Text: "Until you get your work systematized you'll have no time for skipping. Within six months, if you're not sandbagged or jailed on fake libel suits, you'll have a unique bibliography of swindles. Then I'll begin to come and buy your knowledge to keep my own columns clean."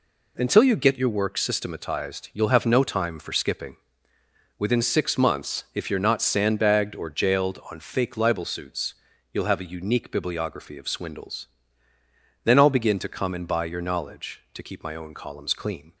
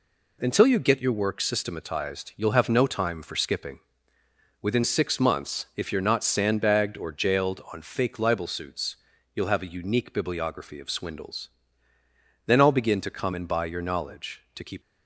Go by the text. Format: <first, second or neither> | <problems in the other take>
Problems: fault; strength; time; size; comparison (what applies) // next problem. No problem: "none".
first | stops before "my own columns clean"; at 14.8 s